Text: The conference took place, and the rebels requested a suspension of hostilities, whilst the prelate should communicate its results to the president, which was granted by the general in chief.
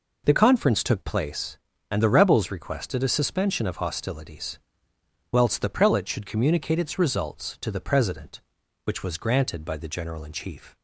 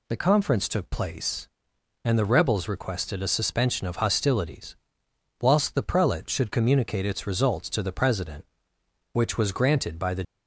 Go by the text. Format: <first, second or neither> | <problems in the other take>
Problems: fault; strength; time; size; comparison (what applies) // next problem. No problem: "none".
first | stops before "general in chief"; at 10.2 s